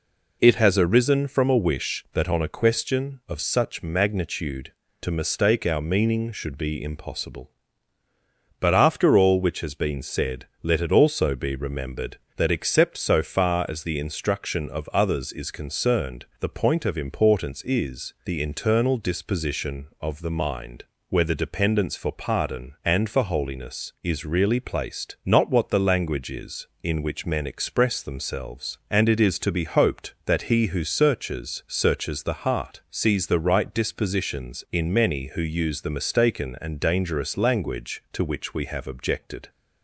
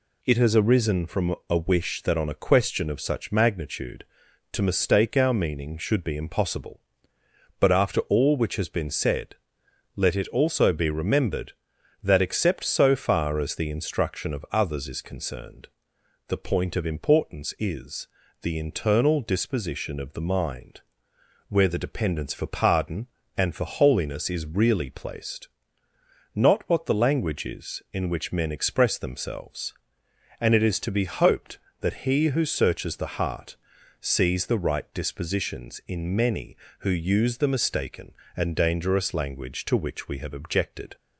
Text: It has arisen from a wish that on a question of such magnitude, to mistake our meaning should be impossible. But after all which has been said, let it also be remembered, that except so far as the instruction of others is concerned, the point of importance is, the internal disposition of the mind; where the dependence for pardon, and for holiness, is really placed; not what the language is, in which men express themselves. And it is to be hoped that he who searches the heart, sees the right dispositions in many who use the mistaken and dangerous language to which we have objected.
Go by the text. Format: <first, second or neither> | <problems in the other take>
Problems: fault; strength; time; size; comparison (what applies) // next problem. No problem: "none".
second | says "searches" twice; at 31.6 s